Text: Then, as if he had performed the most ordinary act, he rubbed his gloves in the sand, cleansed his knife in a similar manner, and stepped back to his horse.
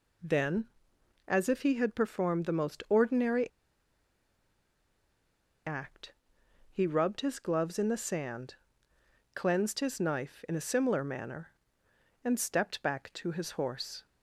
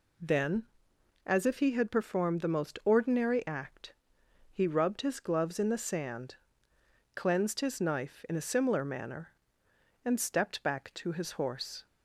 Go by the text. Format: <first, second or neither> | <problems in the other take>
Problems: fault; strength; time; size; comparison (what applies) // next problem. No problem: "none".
second | pauses between "ordinary" and "act"; strong; at 3.5 s; 2.1 s long